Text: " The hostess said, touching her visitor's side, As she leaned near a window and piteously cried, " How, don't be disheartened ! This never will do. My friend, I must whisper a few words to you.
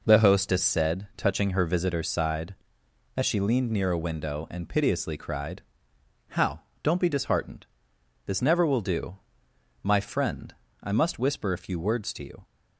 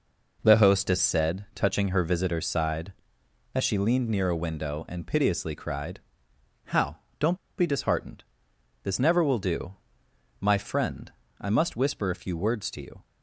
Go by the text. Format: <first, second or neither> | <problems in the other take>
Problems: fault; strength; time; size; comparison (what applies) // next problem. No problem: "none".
first | pauses between "don't" and "be"; slight; at 7.3 s; 0.21 s long